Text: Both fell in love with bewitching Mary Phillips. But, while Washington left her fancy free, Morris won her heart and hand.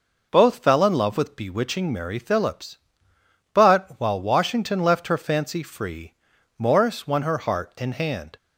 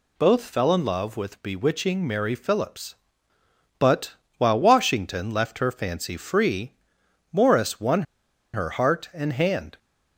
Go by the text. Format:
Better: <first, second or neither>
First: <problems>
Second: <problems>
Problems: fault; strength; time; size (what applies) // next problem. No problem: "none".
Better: first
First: none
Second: pauses between "won" and "her"; noticeable; at 8.0 s; 0.50 s long